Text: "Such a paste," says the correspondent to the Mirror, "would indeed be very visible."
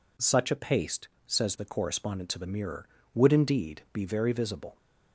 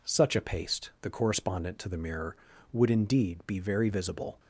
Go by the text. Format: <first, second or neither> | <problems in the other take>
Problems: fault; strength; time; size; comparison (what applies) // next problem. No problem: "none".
first | skips "says"; at 0.9 s